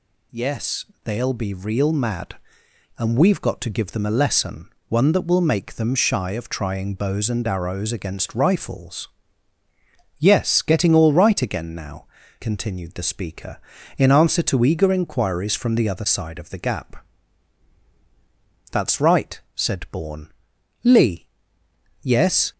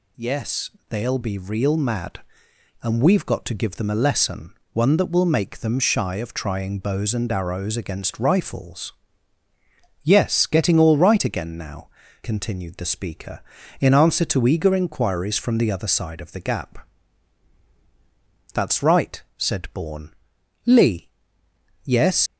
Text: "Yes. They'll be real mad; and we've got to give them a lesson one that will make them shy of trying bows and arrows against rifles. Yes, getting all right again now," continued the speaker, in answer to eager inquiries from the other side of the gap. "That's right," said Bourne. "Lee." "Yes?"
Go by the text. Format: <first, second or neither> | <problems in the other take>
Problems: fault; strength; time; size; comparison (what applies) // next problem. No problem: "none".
first | pauses between "lesson" and "one"; slight; at 4.5 s; 0.18 s long; slight in the first // leaves "Yes" unfinished; at 22.2 s; 80 ms